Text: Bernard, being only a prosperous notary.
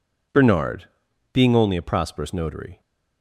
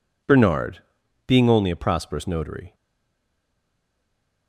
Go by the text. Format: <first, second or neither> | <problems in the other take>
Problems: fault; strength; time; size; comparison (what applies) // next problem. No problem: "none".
first | stays silent after the last word; noticeable; from 2.7 s on; 1.7 s long